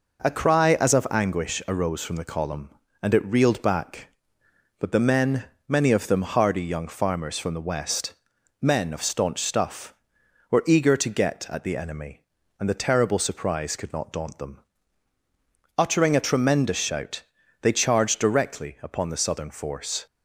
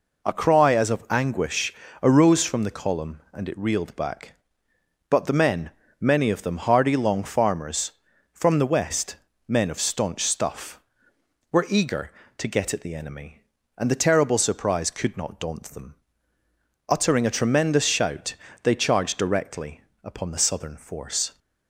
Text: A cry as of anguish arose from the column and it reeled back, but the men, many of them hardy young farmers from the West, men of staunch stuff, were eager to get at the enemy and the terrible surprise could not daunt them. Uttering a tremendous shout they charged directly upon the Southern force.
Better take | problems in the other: first | pauses between "anguish" and "arose"; slight; at 1.7 s; 0.30 s long // says "long" for "young"; at 6.9 s // pauses between "shout" and "they"; slight; at 18.3 s; 0.30 s long; also in the first // pauses between "directly" and "upon"; slight; at 19.8 s; 0.20 s long

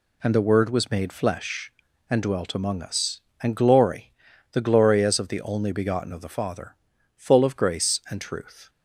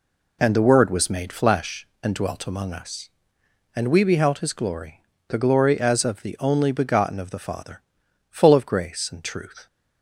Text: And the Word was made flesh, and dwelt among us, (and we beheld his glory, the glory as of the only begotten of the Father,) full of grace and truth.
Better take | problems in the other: second | skips "we beheld his"; at 3.5 s

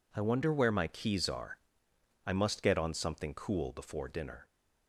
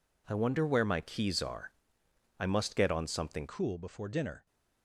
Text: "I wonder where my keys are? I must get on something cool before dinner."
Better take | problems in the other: first | changes voice at "cool"; from 3.4 s on; 1.0 s long

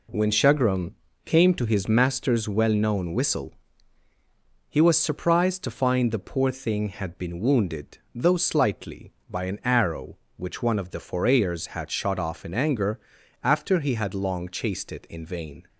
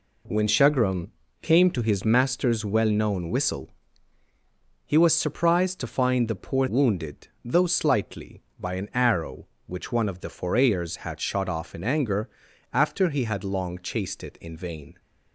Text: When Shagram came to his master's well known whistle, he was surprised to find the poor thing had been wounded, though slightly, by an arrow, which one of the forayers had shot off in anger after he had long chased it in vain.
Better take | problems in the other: first | pauses between "Shagram" and "came"; slight; at 1.1 s; 0.30 s long; slight in the first // skips "thing had been"; at 6.6 s // pauses between "anger" and "after"; at 12.2 s; 0.44 s long; also in the first

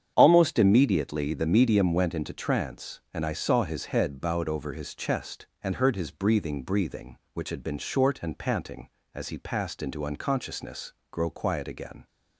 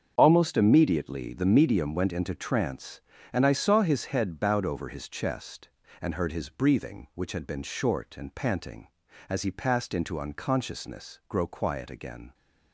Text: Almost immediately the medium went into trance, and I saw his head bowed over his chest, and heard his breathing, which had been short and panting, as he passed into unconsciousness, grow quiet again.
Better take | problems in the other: second | starts louder than the rest; strong; until 1.1 s; 8.5 dB; strong in the second // says "breathing" twice; at 6.6 s

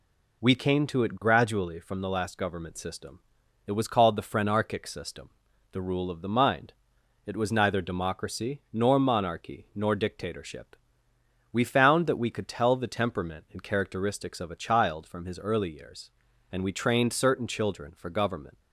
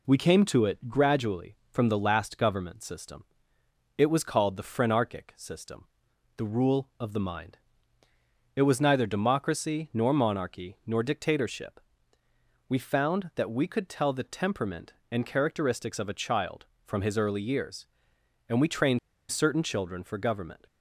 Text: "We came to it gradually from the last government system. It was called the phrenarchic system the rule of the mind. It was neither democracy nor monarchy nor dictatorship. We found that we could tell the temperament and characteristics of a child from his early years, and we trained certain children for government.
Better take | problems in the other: first | pauses between "system" and "the"; noticeable; at 5.8 s; 0.48 s long; also in the first // pauses between "trained" and "certain"; slight; at 18.9 s; 0.30 s long

